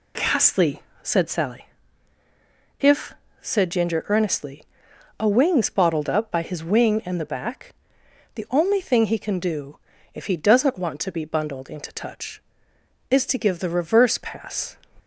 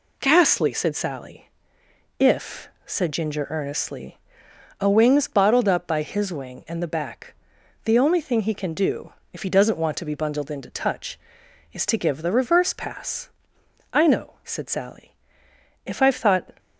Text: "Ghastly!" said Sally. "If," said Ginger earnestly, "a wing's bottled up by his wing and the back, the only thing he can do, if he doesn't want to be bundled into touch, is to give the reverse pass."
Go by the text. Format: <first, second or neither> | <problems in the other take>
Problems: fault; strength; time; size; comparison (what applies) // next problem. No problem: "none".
first | goes on to say "I know said Sally If I've thought"; strong; from 13.9 s on; 2.5 s long